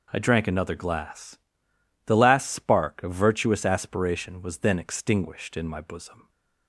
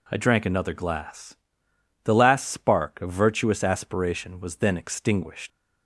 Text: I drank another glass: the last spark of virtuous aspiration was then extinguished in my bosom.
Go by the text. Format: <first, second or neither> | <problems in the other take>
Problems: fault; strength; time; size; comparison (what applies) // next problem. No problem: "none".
first | stops before "in my bosom"; at 5.5 s